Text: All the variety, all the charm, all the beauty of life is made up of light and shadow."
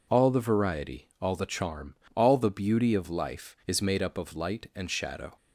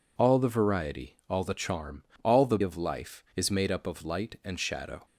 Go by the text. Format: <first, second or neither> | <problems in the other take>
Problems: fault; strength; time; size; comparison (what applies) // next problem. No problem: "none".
first | skips "beauty"; at 2.5 s